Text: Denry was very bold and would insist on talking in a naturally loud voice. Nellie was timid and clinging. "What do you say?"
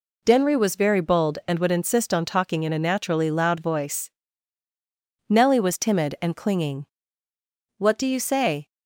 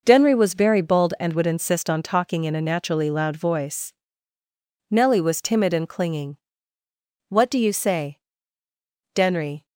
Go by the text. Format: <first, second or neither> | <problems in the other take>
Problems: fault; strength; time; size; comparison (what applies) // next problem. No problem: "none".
first | goes on to say "Denry"; from 9.1 s on; 0.52 s long